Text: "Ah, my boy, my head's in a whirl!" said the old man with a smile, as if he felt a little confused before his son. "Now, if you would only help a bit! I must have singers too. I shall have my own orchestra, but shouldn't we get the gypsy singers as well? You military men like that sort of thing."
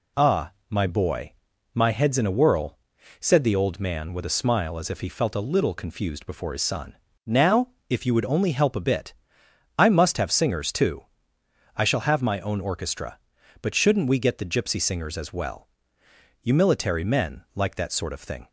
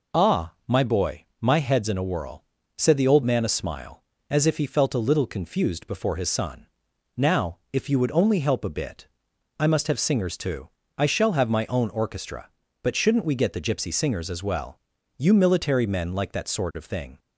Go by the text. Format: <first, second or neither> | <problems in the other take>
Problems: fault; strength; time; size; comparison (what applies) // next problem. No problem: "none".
first | skips "with"; at 3.4 s